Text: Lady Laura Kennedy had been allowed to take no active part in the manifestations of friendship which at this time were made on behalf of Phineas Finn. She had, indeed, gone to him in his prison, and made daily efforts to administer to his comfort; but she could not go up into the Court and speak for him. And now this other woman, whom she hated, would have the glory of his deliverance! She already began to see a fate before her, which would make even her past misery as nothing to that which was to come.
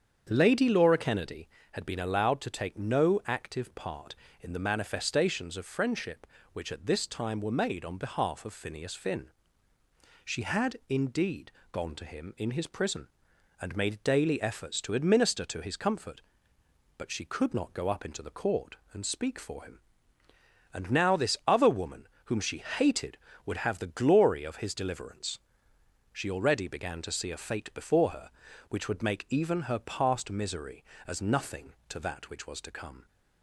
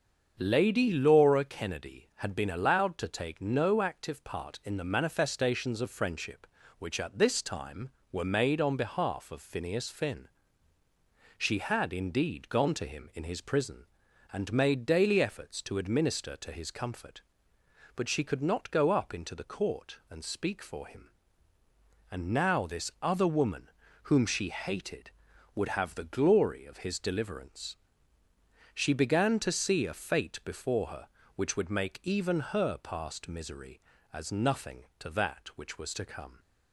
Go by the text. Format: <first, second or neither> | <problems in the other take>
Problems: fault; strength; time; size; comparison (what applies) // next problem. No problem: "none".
first | starts louder than the rest; until 1.4 s; 7 dB; strong in the first // skips "already"; at 28.9 s